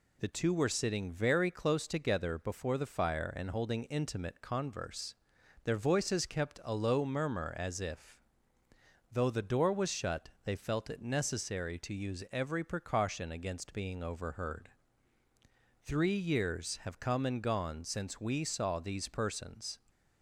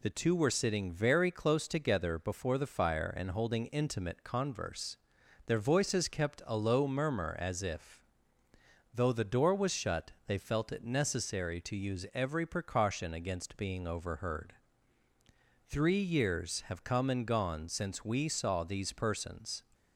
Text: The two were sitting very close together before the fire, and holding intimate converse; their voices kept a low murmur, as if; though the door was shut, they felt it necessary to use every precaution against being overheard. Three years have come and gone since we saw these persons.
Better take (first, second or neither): neither